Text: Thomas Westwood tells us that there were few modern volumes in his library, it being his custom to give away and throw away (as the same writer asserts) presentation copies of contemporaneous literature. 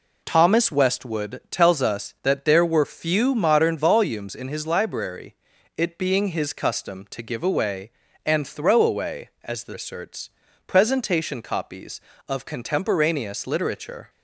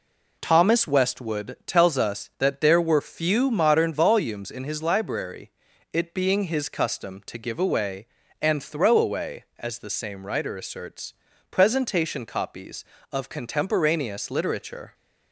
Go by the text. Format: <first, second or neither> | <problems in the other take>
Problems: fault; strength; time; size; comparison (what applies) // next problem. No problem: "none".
second | skips "same writer"; at 9.7 s